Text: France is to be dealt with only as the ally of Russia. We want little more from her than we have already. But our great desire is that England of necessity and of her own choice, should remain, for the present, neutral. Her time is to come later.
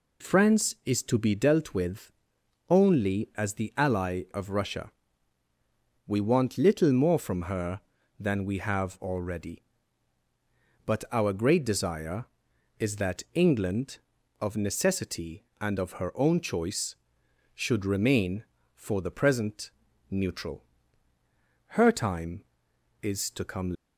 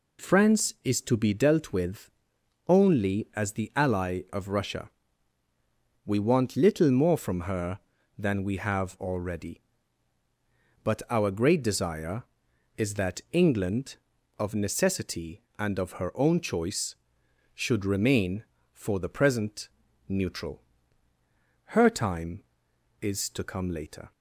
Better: second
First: pauses between "with" and "only"; noticeable; at 2.1 s; 0.58 s long // stops before "later"; at 23.7 s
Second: pauses between "with" and "only"; noticeable; at 2.0 s; 0.58 s long

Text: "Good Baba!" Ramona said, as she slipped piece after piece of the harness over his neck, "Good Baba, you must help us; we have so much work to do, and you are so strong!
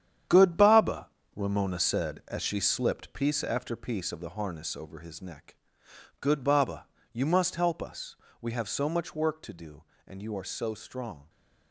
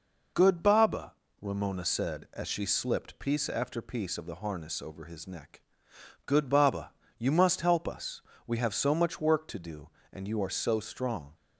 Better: second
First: gets quieter; strong; throughout; 10 dB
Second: none

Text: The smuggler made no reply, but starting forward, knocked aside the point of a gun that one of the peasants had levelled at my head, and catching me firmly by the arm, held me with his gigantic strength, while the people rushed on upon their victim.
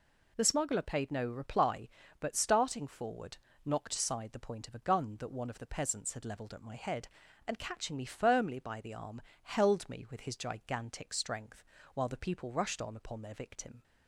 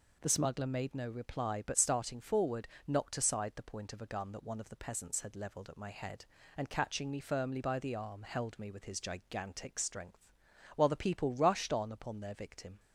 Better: second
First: says "paid" for "made"; at 0.8 s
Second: none

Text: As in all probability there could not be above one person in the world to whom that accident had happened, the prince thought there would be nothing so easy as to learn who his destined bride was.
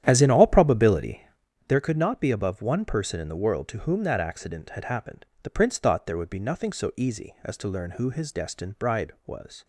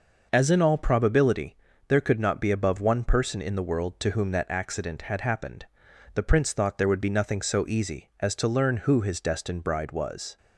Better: second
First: starts louder than the rest; strong; until 1.5 s; 11 dB // pauses between "probability" and "there"; noticeable; at 1.2 s; 0.46 s long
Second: pauses between "probability" and "there"; slight; at 1.5 s; 0.32 s long

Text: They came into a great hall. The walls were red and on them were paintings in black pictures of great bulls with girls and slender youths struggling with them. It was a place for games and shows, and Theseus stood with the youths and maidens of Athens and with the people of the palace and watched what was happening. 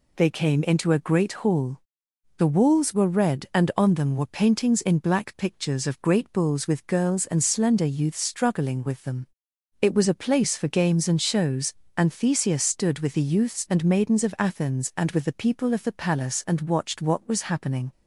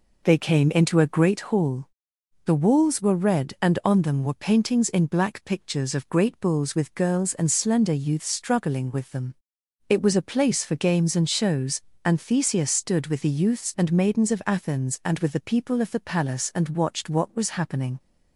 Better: first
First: none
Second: starts louder than the rest; noticeable; until 1.4 s; 4.5 dB

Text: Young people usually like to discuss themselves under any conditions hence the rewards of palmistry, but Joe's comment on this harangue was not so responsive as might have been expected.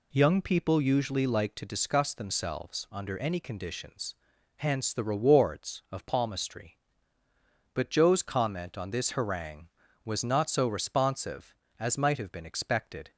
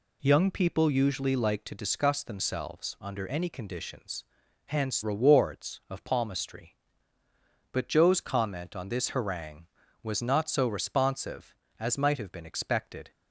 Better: first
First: pauses between "conditions" and "hence"; at 4.1 s; 0.42 s long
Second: pauses between "conditions" and "hence"; at 4.2 s; 0.42 s long // skips "the"; at 5.0 s

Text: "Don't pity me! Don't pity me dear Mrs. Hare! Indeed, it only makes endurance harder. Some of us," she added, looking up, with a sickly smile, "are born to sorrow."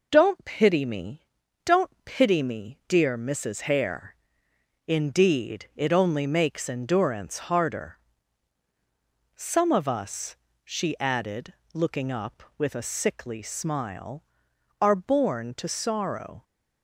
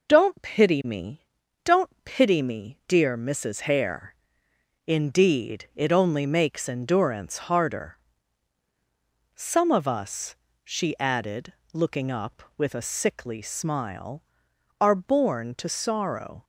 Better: neither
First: none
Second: none

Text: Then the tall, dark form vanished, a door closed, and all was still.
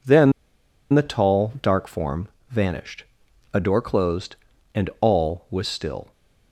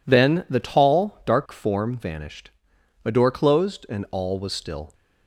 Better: second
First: pauses between "Then" and "the"; noticeable; at 0.3 s; 0.61 s long // pauses between "form" and "vanished"; slight; at 2.2 s; 0.24 s long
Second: none

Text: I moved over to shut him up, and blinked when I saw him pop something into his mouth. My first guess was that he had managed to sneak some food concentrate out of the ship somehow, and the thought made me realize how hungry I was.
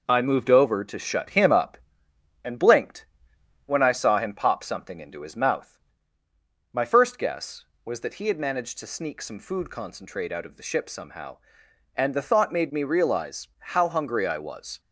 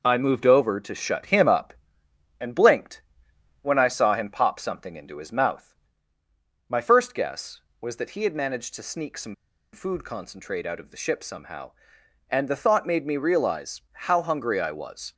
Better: first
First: pauses between "blinked" and "when"; noticeable; at 3.0 s; 0.60 s long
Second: pauses between "blinked" and "when"; noticeable; at 3.0 s; 0.60 s long // pauses between "some" and "food"; at 9.3 s; 0.38 s long

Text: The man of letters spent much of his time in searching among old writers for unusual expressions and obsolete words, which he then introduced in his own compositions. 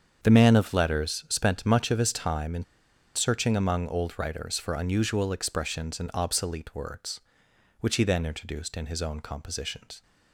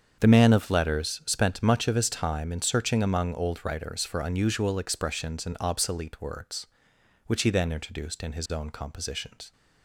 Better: second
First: starts louder than the rest; strong; until 1.2 s; 7 dB // pauses between "in" and "searching"; noticeable; at 2.6 s; 0.51 s long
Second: starts louder than the rest; strong; until 1.2 s; 7 dB

